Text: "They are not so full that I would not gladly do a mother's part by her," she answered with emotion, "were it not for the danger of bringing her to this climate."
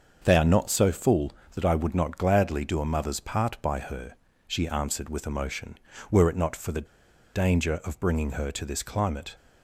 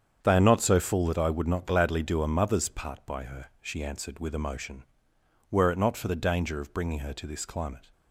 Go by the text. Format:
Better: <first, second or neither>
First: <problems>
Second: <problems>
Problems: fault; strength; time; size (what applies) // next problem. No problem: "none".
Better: second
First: starts louder than the rest; until 1.2 s; 6.5 dB // pauses between "the" and "danger"; noticeable; at 6.8 s; 0.48 s long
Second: starts louder than the rest; strong; until 1.2 s; 8 dB